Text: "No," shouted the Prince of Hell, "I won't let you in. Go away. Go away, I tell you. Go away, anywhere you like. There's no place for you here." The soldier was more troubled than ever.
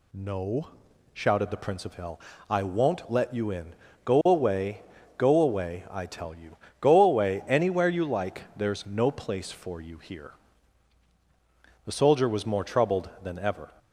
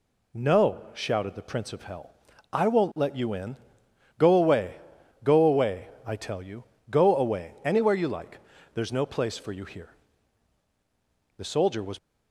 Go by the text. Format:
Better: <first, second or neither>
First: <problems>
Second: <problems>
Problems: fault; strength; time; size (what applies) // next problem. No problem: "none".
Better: first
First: none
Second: stops before "more troubled than ever"; at 11.9 s